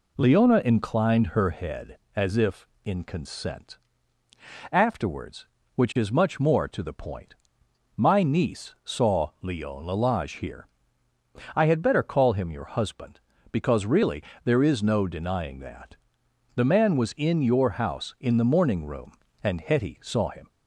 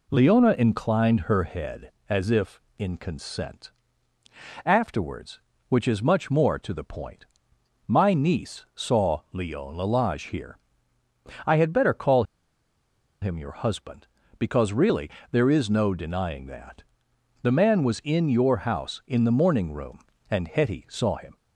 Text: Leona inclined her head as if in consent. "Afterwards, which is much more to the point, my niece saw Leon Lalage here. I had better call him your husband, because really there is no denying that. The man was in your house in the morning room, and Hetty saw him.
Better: first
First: pauses between "really" and "there"; slight; at 14.2 s; 0.20 s long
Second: pauses between "call" and "him"; at 12.2 s; 0.99 s long // pauses between "really" and "there"; slight; at 15.1 s; 0.20 s long

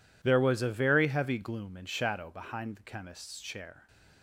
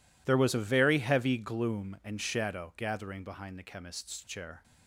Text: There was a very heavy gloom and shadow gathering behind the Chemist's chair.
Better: second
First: skips "gathering"; at 2.2 s // stays silent after the last word; slight; from 3.7 s on; 0.5 s long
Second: none

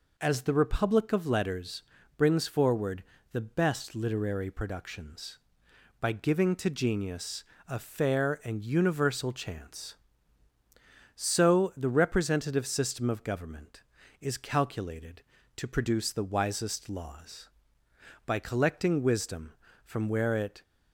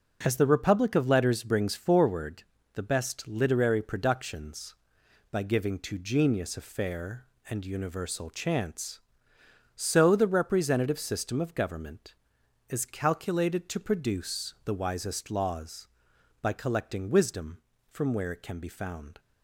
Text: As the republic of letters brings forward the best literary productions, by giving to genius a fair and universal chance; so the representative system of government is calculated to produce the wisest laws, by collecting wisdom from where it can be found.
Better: second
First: pauses between "letters" and "brings"; slight; at 1.8 s; 0.34 s long // pauses between "forward" and "the"; slight; at 3.0 s; 0.30 s long // pauses between "genius" and "a"; slight; at 7.4 s; 0.26 s long // stops before "can be found"; at 20.6 s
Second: pauses between "forward" and "the"; slight; at 2.4 s; 0.32 s long

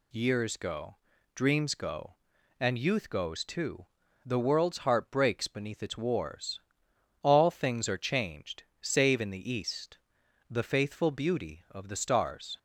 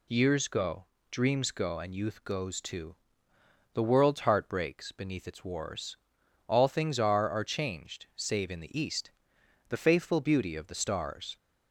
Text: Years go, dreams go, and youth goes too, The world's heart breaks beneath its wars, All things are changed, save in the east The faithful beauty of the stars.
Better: first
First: pauses between "east" and "The"; noticeable; at 9.9 s; 0.54 s long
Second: says "are" twice; at 7.2 s // pauses between "east" and "The"; noticeable; at 9.0 s; 0.58 s long

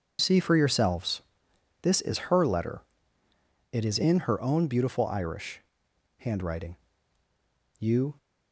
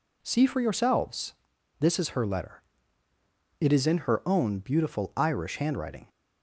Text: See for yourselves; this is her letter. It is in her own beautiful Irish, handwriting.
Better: second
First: goes on to say "You"; slight; from 7.7 s on; 0.38 s long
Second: none

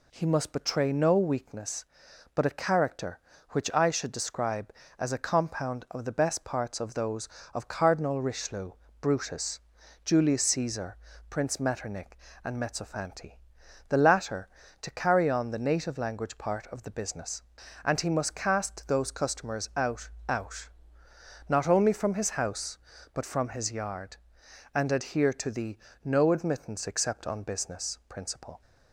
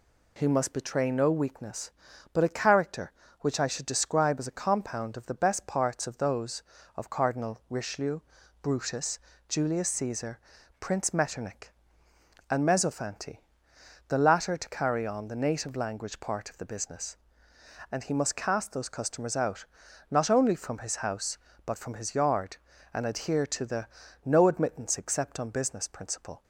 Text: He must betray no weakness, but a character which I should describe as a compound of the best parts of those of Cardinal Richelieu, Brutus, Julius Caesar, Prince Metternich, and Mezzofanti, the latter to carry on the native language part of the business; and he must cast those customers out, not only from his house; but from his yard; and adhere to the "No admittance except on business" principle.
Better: second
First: says "out" twice; at 20.2 s // pauses between "the" and "No"; slight; at 25.7 s; 0.28 s long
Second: pauses between "the" and "No"; slight; at 23.8 s; 0.36 s long

